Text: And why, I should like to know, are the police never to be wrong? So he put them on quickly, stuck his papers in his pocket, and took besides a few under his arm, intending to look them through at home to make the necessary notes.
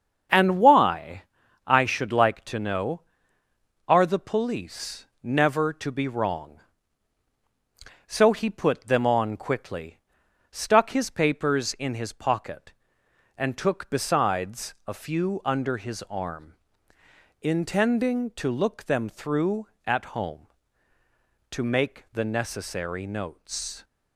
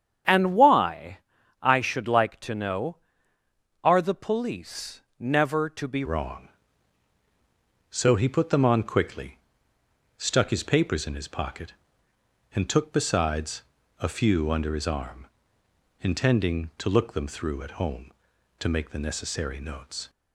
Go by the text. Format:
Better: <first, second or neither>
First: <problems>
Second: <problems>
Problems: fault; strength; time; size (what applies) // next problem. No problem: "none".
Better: first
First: starts louder than the rest; strong; until 1.7 s; 7.5 dB // pauses between "police" and "never"; slight; at 5.0 s; 0.17 s long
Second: starts louder than the rest; strong; until 1.7 s; 8.5 dB // pauses between "police" and "never"; slight; at 5.0 s; 0.18 s long // changes voice at "wrong"; from 6.0 s on; 14.0 s long // pauses between "besides" and "a"; at 13.6 s; 0.38 s long